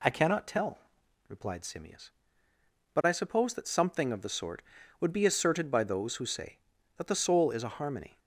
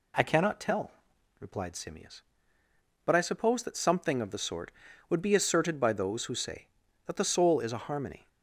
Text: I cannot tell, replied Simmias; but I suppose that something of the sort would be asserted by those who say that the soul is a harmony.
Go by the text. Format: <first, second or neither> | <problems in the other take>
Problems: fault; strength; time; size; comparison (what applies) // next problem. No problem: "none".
neither | none